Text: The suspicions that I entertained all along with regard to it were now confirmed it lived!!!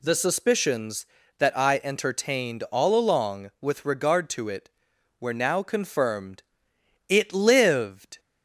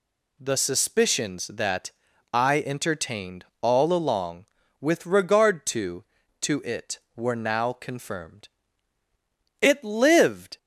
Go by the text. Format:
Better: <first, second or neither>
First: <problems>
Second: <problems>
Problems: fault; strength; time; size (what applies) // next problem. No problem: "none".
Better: first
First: pauses between "confirmed" and "it"; noticeable; at 6.4 s; 0.66 s long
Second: pauses between "that" and "I"; at 1.9 s; 0.42 s long // pauses between "entertained" and "all"; slight; at 3.4 s; 0.16 s long // says "to" twice; at 6.4 s // pauses between "confirmed" and "it"; at 8.4 s; 1.1 s long